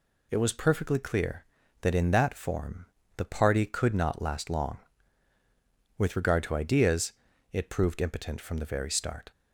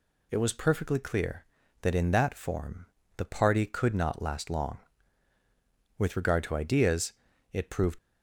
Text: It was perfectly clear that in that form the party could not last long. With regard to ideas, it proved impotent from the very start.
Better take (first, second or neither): first